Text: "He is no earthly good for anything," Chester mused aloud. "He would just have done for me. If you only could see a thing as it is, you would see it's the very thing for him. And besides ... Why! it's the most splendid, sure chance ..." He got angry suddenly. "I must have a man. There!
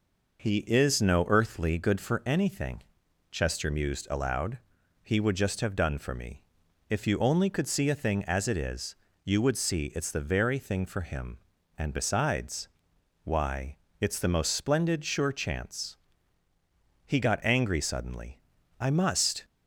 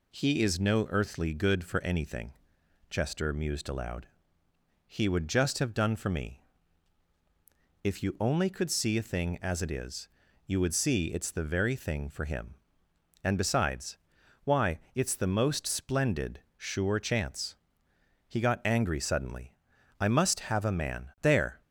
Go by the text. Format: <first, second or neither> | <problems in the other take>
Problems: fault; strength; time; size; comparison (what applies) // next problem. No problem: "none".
second | stops before "have a man There"; at 19.4 s